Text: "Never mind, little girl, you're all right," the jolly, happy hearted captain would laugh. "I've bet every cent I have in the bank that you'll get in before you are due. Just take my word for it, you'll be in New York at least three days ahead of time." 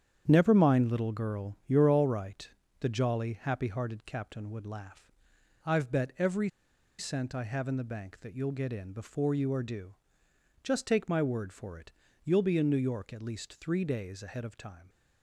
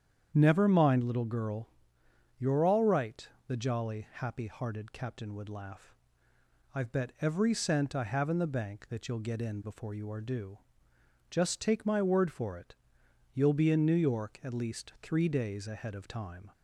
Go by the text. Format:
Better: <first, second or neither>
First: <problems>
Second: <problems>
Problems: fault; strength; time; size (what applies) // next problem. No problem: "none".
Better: second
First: starts louder than the rest; strong; until 1.2 s; 9 dB // pauses between "every" and "cent"; noticeable; at 6.4 s; 0.50 s long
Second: starts louder than the rest; strong; until 1.3 s; 8.5 dB